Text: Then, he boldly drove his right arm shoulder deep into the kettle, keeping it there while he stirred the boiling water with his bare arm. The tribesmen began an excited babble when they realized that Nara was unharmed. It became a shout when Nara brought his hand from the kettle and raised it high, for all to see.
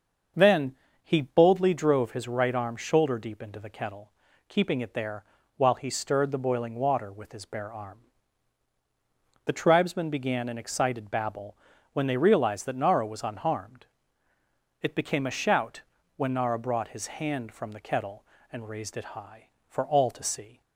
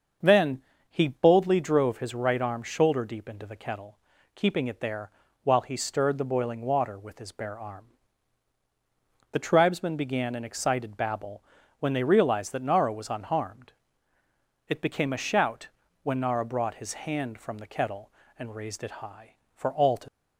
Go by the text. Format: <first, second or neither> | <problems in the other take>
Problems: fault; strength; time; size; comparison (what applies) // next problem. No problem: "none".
first | starts louder than the rest; until 1.5 s; 6.5 dB; also in the first // pauses between "there" and "while"; slight; at 5.0 s; 0.34 s long; slight in the first // pauses between "babble" and "when"; at 11.4 s; 0.38 s long; also in the first // pauses between "shout" and "when"; slight; at 15.6 s; 0.36 s long; slight in the first // stops before "see"; at 20.0 s